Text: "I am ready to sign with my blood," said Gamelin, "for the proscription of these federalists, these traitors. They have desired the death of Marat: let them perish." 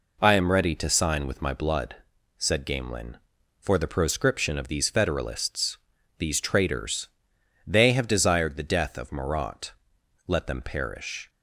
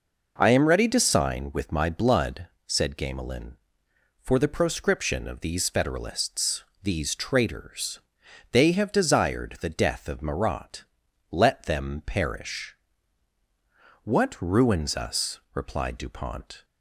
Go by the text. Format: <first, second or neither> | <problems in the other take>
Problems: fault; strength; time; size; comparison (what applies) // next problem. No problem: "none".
first | goes on to say "What ruins us replied Dupont"; strong; from 14.0 s on; 2.6 s long